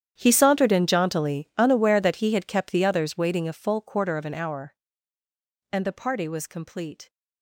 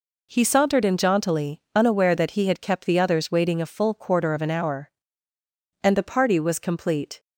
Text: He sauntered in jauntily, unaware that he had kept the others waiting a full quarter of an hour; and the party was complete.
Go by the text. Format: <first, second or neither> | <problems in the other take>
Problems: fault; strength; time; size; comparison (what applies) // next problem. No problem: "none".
second | gets quieter; strong; throughout; 19 dB